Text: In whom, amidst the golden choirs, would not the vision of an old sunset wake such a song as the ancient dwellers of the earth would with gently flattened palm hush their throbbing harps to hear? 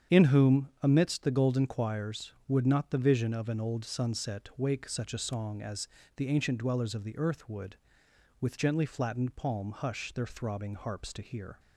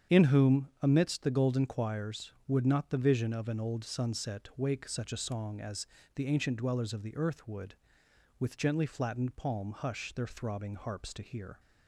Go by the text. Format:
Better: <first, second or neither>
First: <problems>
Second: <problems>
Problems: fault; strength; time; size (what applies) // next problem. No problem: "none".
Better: neither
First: starts louder than the rest; strong; until 1.2 s; 8 dB // pauses between "as" and "the"; slight; at 5.8 s; 0.30 s long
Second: starts louder than the rest; strong; until 1.2 s; 8 dB // pauses between "as" and "the"; slight; at 5.8 s; 0.30 s long